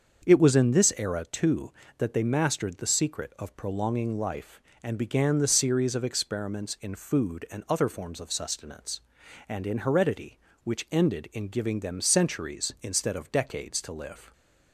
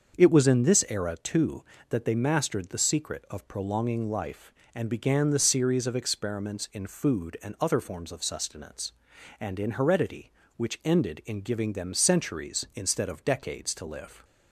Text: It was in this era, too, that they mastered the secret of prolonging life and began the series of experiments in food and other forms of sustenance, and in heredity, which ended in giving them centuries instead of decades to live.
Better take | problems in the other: neither | starts louder than the rest; the same in both

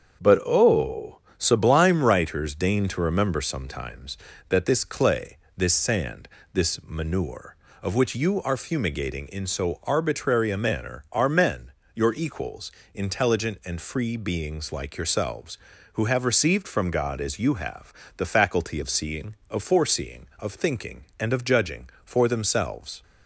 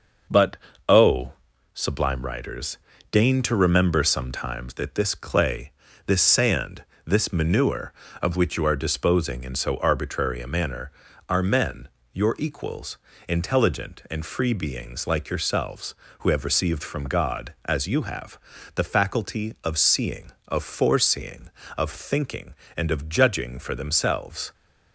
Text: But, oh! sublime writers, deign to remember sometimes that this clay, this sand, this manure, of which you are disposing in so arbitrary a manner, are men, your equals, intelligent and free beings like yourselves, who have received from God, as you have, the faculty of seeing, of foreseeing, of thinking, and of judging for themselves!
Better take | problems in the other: second | starts louder than the rest; strong; until 1.4 s; 7 dB // says "fumigating" for "disposing"; at 8.5 s

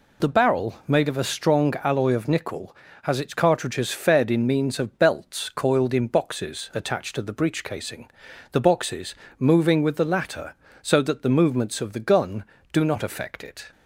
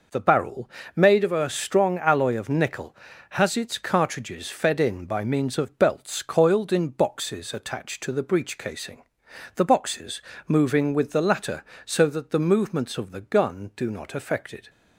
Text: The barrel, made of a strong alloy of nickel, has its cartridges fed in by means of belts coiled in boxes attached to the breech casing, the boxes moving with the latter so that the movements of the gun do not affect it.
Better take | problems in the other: second | skips "by"; at 4.4 s // pauses between "boxes" and "moving"; slight; at 9.1 s; 0.24 s long; slight in the second

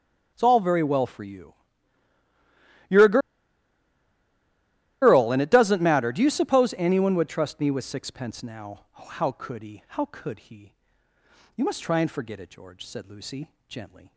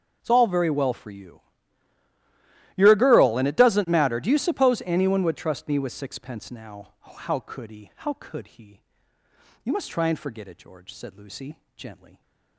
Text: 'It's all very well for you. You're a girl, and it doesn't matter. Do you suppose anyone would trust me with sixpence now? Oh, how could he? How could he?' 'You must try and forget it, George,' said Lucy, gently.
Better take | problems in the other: second | starts louder than the rest; until 1.3 s; 6.5 dB; also in the second // pauses between "a" and "girl"; strong; at 3.1 s; 1.8 s long

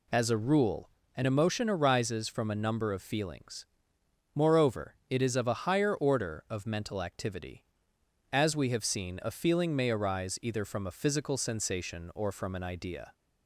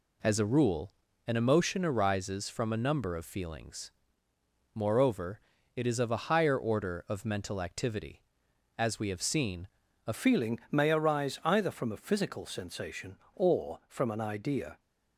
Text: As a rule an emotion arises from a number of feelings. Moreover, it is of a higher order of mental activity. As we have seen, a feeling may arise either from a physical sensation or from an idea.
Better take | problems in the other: first | pauses between "rule" and "an"; slight; at 0.9 s; 0.36 s long; slight in the first // changes voice at "feeling"; from 10.1 s on; 4.6 s long

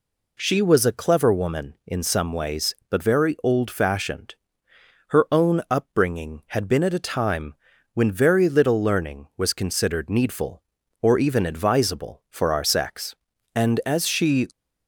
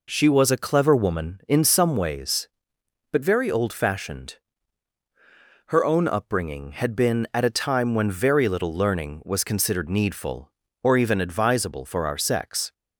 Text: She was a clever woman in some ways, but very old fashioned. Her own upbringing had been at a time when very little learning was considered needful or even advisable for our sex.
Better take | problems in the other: second | pauses between "time" and "when"; at 7.5 s; 0.40 s long // goes on to say "And as she"; noticeable; from 13.5 s on; 0.92 s long

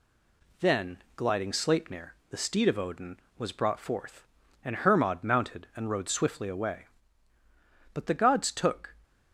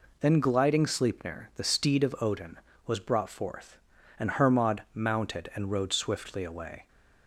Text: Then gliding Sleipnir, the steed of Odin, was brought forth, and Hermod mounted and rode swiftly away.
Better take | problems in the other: second | goes on to say "But the gods took"; noticeable; from 7.9 s on; 1.0 s long

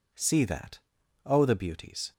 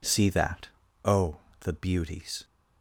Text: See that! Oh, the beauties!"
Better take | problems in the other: neither | none

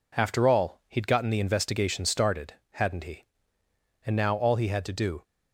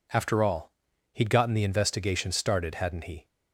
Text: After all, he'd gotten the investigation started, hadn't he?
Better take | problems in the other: second | goes on to say "And now all he had to do"; noticeable; from 4.0 s on; 1.1 s long

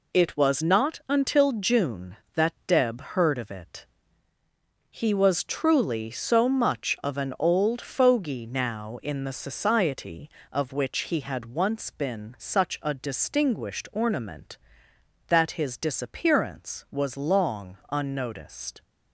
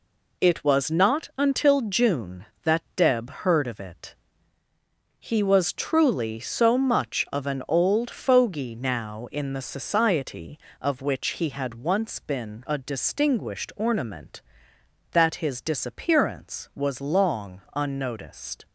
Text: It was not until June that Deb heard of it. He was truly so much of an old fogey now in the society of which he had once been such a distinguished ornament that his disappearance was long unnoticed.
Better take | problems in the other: first | skips "such"; at 12.6 s

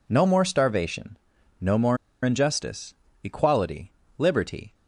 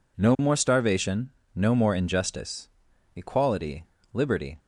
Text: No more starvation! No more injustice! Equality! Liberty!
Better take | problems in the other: second | pauses between "more" and "injustice"; slight; at 1.9 s; 0.27 s long

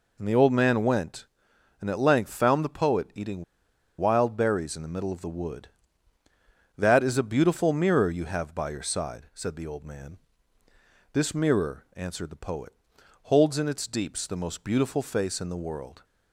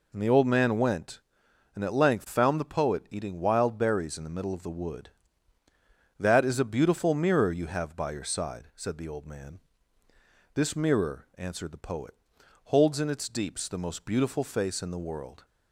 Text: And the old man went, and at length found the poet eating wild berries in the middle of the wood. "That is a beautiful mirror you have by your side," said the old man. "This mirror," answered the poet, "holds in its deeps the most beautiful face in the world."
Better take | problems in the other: second | pauses between "eating" and "wild"; noticeable; at 3.4 s; 0.55 s long

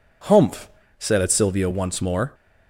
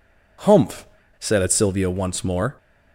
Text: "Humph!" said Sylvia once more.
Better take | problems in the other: neither | none

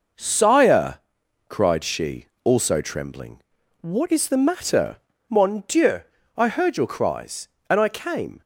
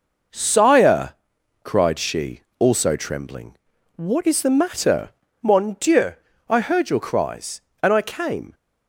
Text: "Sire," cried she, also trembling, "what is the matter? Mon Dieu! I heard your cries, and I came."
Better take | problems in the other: neither | none

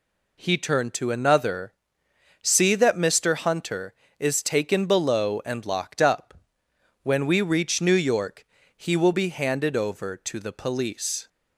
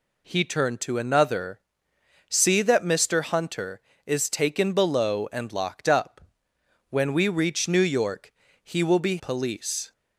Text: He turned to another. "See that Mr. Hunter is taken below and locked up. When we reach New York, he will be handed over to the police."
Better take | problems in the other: first | skips "handed over to the"; at 9.1 s

